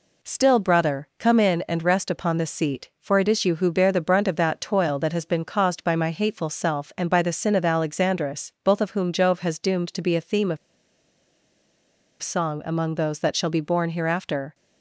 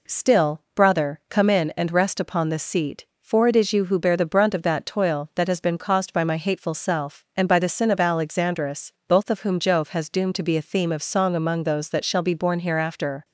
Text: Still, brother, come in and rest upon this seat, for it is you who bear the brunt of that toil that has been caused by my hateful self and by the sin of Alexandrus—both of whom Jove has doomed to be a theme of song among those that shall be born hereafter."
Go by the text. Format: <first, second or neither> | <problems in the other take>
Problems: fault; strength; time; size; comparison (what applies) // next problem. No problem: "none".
second | pauses between "of" and "song"; strong; at 10.5 s; 1.6 s long